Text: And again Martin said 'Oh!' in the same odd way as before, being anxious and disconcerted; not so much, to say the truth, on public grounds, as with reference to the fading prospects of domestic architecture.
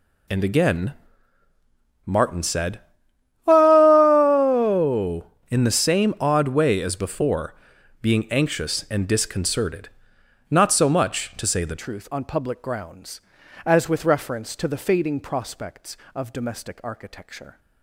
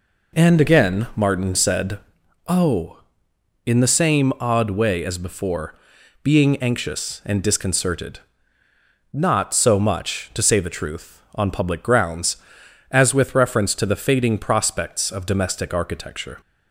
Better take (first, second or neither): second